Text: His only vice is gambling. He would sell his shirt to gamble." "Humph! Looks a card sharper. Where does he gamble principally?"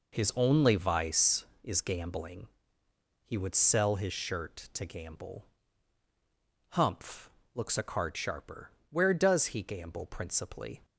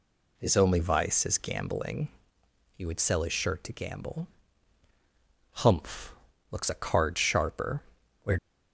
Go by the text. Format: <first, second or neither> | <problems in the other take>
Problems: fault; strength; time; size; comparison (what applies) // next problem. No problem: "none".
first | stops before "does he gamble principally"; at 8.3 s